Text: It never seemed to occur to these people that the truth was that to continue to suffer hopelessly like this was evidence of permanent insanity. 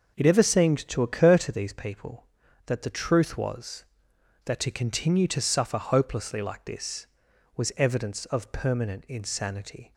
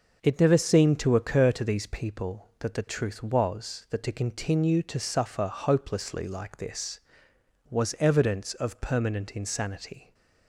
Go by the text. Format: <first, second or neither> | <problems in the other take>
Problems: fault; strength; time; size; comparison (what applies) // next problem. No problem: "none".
second | says "ever" for "never"; at 0.2 s